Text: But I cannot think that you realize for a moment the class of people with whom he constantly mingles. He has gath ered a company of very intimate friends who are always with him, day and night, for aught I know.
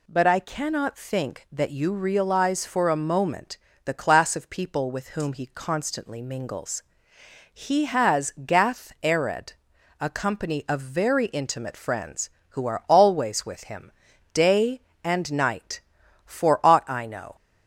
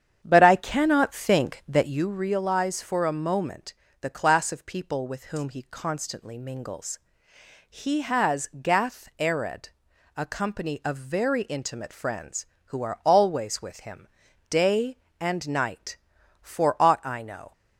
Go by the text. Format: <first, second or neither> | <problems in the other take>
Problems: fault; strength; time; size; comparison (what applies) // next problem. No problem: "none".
first | starts louder than the rest; strong; until 2.1 s; 8.5 dB // pauses between "moment" and "the"; slight; at 3.7 s; 0.26 s long; slight in the first // pauses between "ered" and "a"; noticeable; at 9.6 s; 0.48 s long; noticeable in the first